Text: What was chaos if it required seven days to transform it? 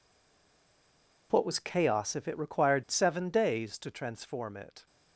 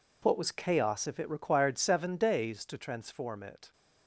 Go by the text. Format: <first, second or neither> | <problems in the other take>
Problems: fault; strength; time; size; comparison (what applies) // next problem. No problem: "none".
second | stays silent before the first word; noticeable; until 1.3 s; 1.3 s long